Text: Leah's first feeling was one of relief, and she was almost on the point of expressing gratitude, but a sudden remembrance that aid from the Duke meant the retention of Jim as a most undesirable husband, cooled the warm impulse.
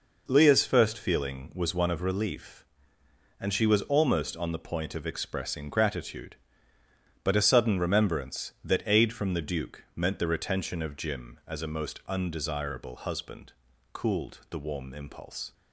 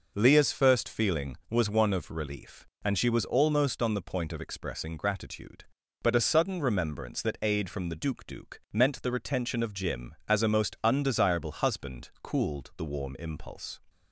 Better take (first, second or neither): first